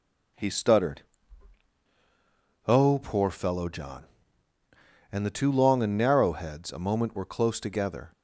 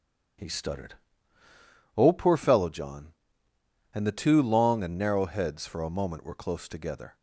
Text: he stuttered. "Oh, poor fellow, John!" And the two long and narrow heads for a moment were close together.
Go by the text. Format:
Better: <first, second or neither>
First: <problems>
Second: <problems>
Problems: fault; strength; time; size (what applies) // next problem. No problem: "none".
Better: second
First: skips "for"; at 6.7 s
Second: none